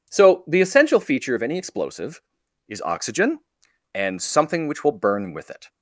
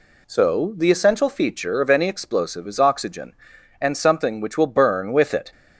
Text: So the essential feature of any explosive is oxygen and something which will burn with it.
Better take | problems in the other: neither | none

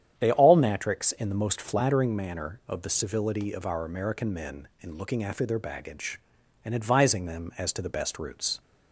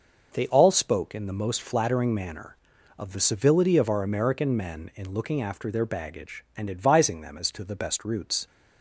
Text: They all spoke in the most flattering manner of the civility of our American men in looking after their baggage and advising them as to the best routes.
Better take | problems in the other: second | starts louder than the rest; strong; until 1.2 s; 9.5 dB // says "natrix" for "spoke"; at 0.5 s

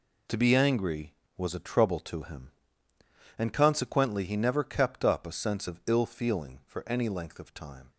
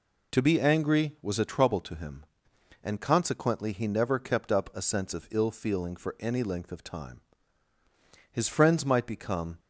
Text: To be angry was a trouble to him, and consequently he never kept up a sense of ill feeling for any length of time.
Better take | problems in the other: first | goes on to say "His friends might become"; noticeable; from 8.3 s on; 1.2 s long

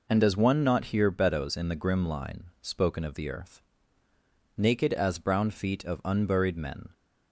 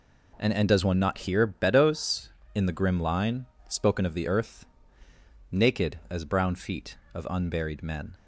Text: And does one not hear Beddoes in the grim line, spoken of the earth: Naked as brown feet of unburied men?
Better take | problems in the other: first | says "And" twice; at 0.5 s

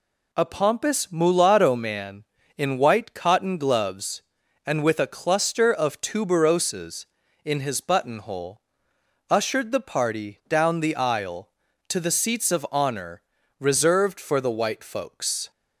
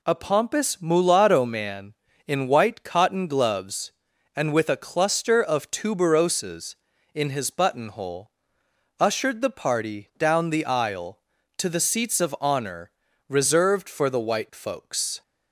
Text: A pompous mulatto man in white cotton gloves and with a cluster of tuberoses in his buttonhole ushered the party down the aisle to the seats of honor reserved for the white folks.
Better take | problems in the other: neither | pauses between "buttonhole" and "ushered"; noticeable; the same in both // pauses between "honor" and "reserved"; the same in both

